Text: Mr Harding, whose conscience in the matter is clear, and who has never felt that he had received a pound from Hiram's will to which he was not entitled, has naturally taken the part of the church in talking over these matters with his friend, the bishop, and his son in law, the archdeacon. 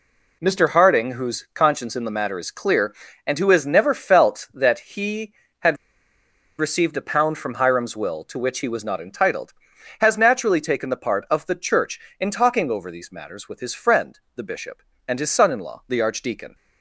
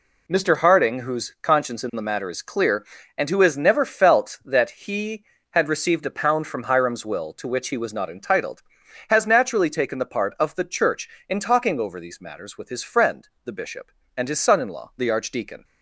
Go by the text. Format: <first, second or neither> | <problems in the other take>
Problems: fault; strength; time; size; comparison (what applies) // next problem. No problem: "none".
second | pauses between "had" and "received"; noticeable; at 5.7 s; 0.82 s long